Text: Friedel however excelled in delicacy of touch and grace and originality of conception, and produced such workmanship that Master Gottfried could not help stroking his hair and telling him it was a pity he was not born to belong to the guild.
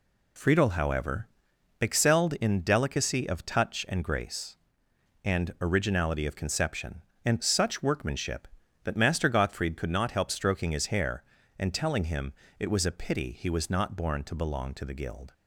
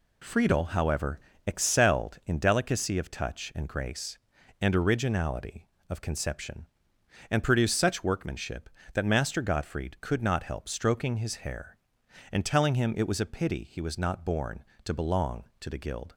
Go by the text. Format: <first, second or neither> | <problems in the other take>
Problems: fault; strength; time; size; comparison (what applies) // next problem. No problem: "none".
second | pauses between "however" and "excelled"; noticeable; at 1.2 s; 0.54 s long; slight in the second // skips "produced"; at 7.4 s // pauses between "him" and "it"; slight; at 12.3 s; 0.26 s long